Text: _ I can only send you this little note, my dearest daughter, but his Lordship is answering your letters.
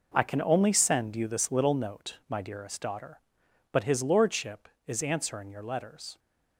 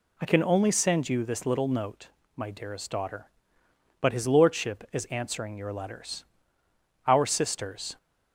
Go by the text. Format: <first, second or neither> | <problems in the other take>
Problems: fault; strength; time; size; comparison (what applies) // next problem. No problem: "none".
first | goes on to say "Our Sisters"; noticeable; from 7.0 s on; 0.90 s long